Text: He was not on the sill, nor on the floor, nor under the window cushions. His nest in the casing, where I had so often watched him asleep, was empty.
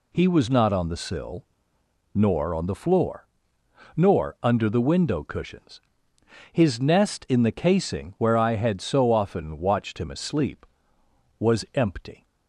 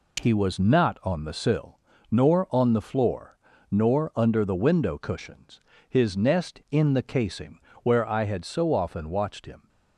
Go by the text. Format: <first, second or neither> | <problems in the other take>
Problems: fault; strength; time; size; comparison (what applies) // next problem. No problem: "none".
first | stops before "asleep was empty"; at 9.6 s